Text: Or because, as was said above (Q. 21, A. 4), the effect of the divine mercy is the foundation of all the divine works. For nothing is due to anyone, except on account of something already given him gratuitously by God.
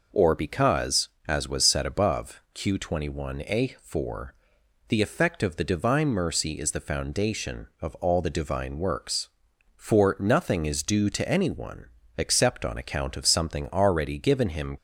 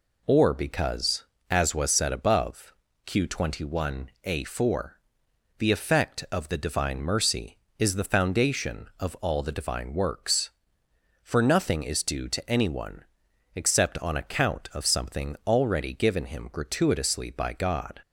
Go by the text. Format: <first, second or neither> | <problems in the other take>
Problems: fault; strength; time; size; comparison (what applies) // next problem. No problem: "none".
second | stops before "gratuitously by God"; at 14.7 s